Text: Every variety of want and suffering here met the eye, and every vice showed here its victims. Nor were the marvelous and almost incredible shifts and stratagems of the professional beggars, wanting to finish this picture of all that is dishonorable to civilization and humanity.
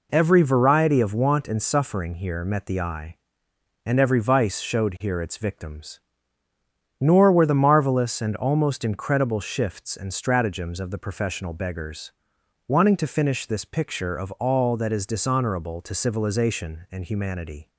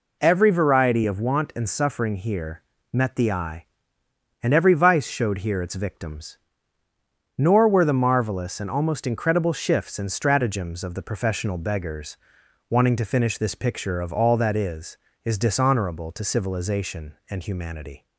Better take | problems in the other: first | pauses between "here" and "met"; slight; at 2.6 s; 0.32 s long // says "is" twice; at 15.2 s

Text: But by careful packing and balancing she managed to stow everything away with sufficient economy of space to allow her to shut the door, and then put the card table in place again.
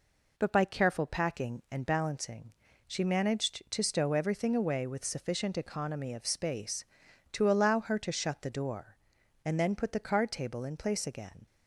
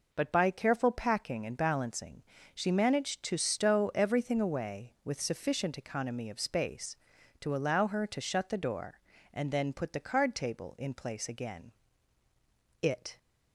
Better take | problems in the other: first | pauses between "balancing" and "she"; slight; at 2.2 s; 0.32 s long; slight in the first // goes on to say "It"; slight; from 12.8 s on; 0.36 s long

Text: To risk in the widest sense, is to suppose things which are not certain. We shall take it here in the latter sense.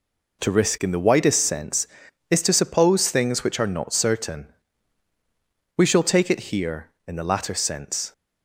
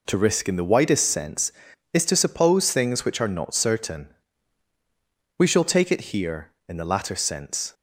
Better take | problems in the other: neither | none

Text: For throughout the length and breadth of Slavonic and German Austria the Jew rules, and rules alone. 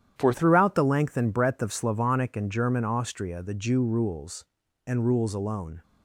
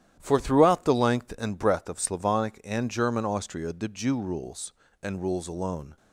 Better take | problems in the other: second | starts louder than the rest; strong; until 1.1 s; 10 dB; strong in the second // changes voice at "throughout"; from 0.3 s on; 5.5 s long

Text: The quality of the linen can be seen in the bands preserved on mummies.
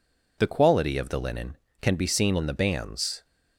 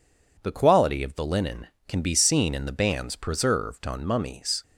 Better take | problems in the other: second | stops before "preserved on mummies"; at 3.2 s

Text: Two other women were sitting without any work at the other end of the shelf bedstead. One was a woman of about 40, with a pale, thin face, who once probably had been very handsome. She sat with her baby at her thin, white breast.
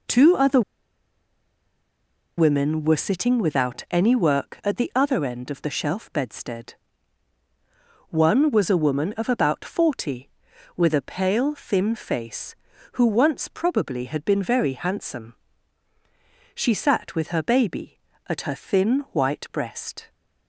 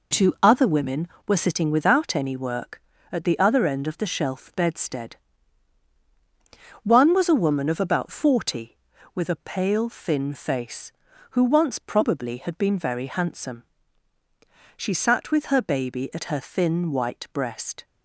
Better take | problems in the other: second | pauses between "other" and "women"; strong; at 0.6 s; 1.7 s long

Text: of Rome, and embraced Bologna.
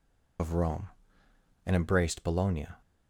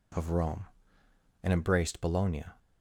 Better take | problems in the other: second | loses the start of "of"; at 0.3 s; 50 ms

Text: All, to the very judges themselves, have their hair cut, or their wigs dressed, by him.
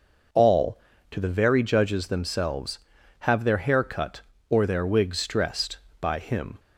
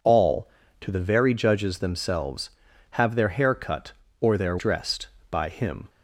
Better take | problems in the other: first | skips "wigs"; at 4.5 s

